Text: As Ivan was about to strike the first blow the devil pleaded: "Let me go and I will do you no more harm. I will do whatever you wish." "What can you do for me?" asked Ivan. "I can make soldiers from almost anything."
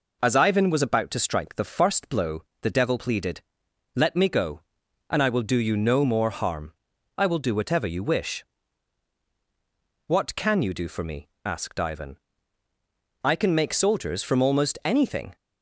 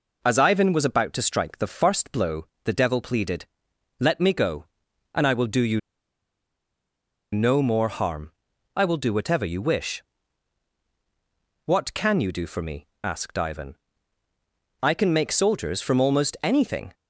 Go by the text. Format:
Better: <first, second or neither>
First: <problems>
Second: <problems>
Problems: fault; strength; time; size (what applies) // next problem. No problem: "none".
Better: first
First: pauses between "blow" and "the"; slight; at 2.4 s; 0.18 s long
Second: pauses between "blow" and "the"; slight; at 2.4 s; 0.18 s long // pauses between "you" and "no"; strong; at 5.7 s; 1.5 s long